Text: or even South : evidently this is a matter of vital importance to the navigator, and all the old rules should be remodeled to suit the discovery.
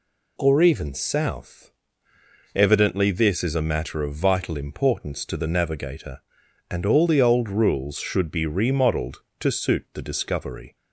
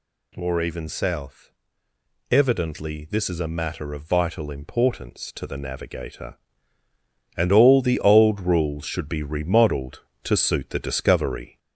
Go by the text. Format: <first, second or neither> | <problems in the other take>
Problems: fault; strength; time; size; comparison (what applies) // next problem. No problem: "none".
first | gets louder; slight; throughout; 2 dB